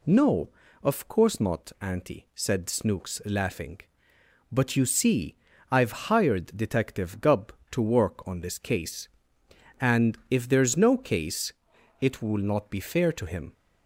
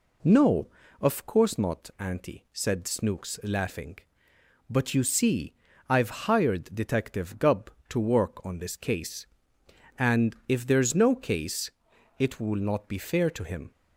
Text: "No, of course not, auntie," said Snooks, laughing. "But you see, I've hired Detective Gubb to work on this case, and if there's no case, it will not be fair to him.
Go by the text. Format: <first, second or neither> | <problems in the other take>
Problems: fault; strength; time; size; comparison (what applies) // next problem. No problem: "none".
first | starts louder than the rest; slight; until 1.5 s; 3 dB